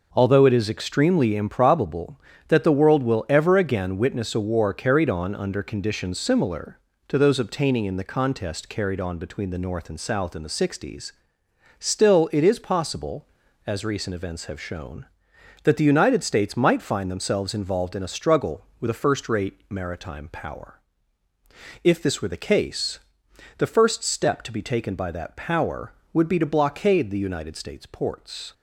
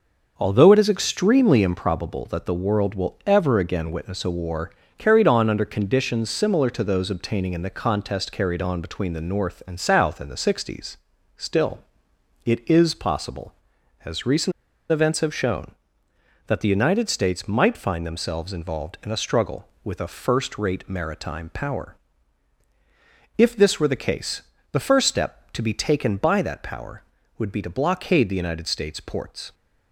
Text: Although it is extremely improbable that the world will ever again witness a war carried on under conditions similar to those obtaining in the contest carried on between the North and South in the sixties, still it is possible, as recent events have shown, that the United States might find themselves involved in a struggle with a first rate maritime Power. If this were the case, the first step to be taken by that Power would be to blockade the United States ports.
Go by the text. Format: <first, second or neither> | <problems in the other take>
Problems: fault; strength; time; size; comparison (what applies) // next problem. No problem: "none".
first | starts louder than the rest; noticeable; until 1.3 s; 6 dB // pauses between "war" and "carried"; slight; at 4.6 s; 0.28 s long // pauses between "still" and "it"; noticeable; at 11.7 s; 0.64 s long // pauses between "recent" and "events"; at 14.5 s; 0.39 s long